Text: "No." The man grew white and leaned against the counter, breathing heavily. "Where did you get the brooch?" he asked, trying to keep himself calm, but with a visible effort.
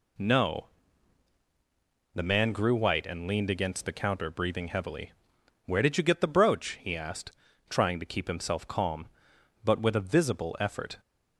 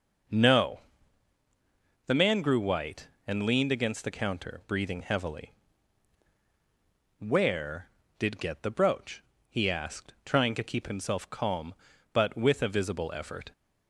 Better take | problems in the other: first | skips "you"; at 8.4 s

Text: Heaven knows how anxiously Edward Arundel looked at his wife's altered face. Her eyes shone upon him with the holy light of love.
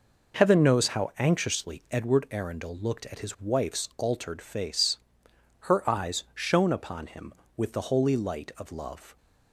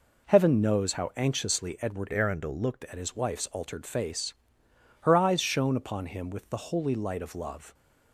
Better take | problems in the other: first | changes voice from "Arundel" to "looked"; from 2.1 to 2.8 s; 0.7 s long

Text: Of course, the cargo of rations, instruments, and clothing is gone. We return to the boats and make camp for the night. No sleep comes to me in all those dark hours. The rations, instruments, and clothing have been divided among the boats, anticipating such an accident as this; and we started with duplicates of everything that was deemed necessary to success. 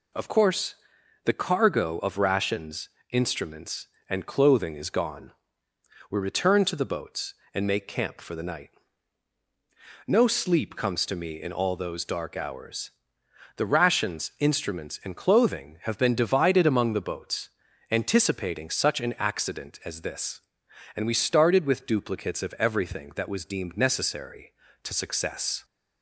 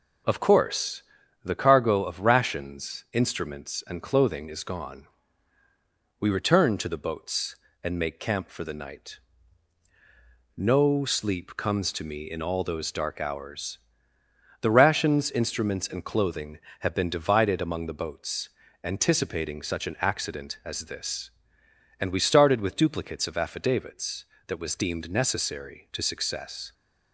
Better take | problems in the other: first | says "affidavits" for "everything"; at 23.3 s

